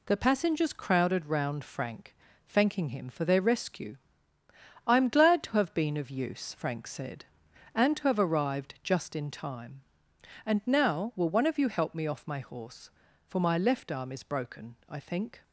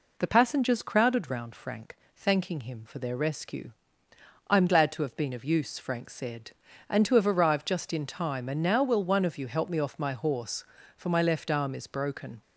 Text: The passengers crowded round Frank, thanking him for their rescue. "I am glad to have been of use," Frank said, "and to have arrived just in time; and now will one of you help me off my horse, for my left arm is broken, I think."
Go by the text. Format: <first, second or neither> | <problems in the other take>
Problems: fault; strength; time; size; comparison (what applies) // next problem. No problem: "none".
first | stops before "I think"; at 12.4 s